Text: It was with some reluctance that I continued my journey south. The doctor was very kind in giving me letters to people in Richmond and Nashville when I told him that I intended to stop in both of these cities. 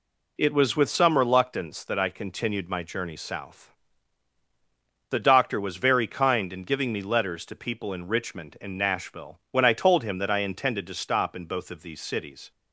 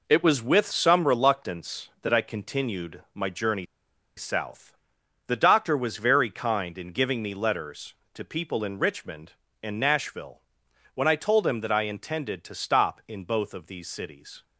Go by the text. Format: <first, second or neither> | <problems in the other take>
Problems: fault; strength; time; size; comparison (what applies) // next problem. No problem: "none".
first | pauses between "journey" and "south"; noticeable; at 3.6 s; 0.52 s long // pauses between "Nashville" and "when"; noticeable; at 10.3 s; 0.54 s long